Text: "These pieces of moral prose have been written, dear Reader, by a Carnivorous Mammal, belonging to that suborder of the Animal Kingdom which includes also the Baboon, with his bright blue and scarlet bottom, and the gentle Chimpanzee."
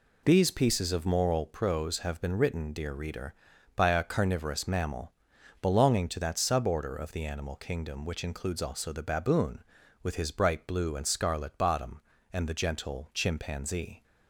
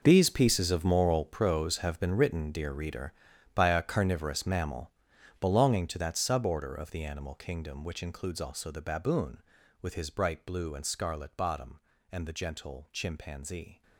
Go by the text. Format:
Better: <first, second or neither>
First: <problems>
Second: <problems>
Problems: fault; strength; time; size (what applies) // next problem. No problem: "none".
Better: first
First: none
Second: gets quieter; strong; throughout; 15 dB